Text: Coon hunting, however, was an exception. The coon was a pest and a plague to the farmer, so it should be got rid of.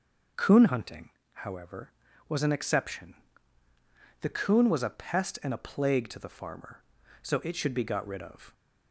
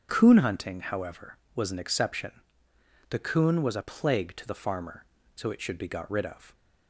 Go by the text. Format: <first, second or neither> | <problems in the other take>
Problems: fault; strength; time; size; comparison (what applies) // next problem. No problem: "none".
first | starts louder than the rest; until 1.1 s; 6.5 dB // skips "pest and a"; at 3.8 s